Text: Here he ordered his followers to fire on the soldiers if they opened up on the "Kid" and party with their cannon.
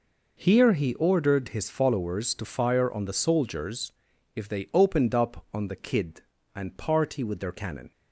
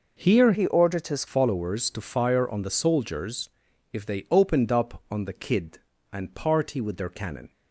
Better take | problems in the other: first | changes voice from "he" to "his"; from 0.5 to 1.2 s; 0.7 s long // pauses between "soldiers" and "if"; at 3.4 s; 0.42 s long; also in the first

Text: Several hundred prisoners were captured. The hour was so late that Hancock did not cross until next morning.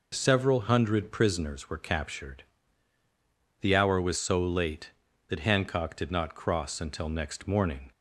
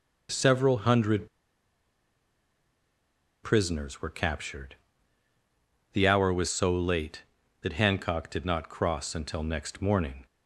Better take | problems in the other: first | pauses between "hundred" and "prisoners"; strong; at 1.2 s; 2.1 s long

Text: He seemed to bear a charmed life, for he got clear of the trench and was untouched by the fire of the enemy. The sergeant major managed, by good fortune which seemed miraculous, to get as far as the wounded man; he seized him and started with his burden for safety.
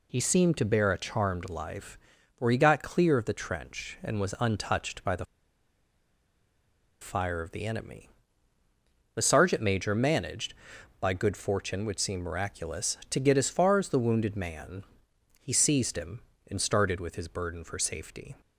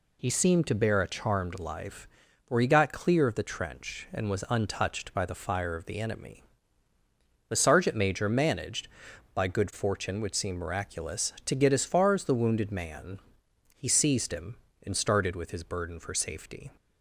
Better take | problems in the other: second | pauses between "the" and "fire"; strong; at 5.2 s; 1.7 s long

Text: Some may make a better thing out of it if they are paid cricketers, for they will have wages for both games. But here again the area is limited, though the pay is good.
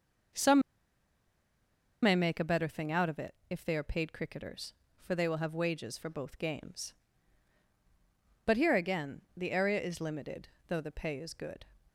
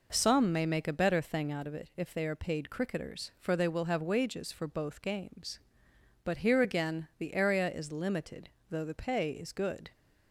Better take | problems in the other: second | pauses between "Some" and "may"; strong; at 0.6 s; 1.4 s long

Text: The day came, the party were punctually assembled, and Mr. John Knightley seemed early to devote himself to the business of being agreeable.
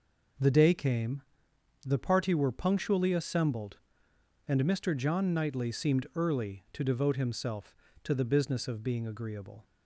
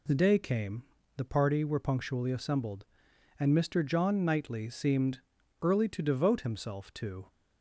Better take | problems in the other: first | pauses between "seemed" and "early"; at 5.1 s; 0.42 s long // stops before "the business of being agreeable"; at 7.2 s

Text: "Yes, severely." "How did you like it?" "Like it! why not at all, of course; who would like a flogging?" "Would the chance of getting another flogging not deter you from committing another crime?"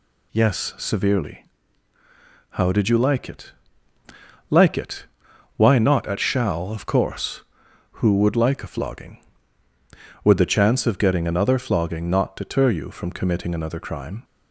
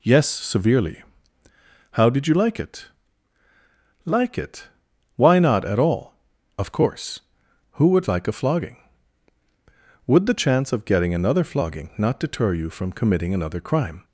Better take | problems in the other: second | says "shall" for "all"; at 6.1 s

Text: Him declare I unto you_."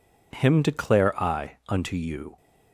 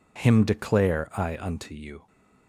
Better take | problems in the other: neither | none

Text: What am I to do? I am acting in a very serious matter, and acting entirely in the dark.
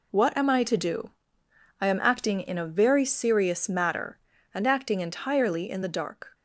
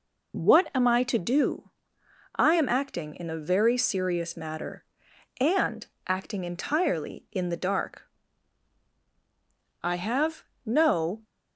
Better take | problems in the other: first | pauses between "and" and "acting"; slight; at 5.8 s; 0.22 s long // goes on to say "I have no"; from 9.8 s on; 1.4 s long

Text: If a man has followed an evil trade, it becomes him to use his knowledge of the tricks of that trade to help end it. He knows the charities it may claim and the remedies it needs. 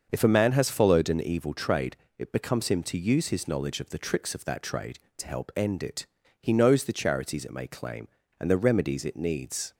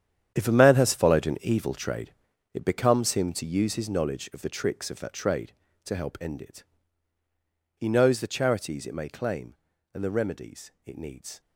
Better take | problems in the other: first | gets quieter; strong; throughout; 13 dB // starts louder than the rest; strong; until 1.3 s; 9.5 dB; also in the first

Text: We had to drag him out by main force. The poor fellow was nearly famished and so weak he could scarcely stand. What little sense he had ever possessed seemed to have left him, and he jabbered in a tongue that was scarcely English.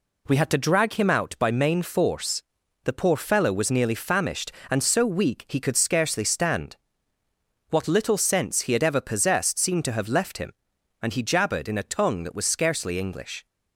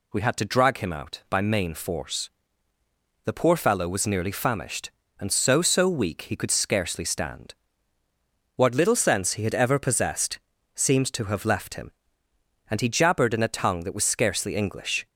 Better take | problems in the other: first | says "so" twice; at 5.6 s // pauses between "possessed" and "seemed"; slight; at 10.3 s; 0.34 s long

